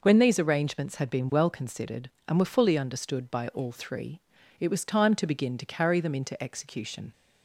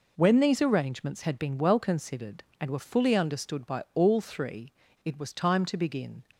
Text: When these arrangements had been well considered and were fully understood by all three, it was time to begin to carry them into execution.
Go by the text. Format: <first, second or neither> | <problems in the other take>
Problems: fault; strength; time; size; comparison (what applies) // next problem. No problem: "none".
first | stops before "to carry them into execution"; at 6.3 s